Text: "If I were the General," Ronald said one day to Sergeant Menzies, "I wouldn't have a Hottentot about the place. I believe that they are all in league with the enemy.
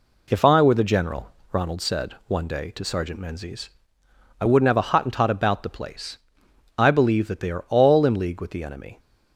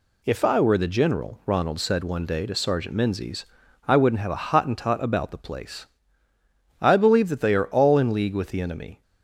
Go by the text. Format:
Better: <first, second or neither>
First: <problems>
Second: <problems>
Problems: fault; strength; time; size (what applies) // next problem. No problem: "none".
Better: neither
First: none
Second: none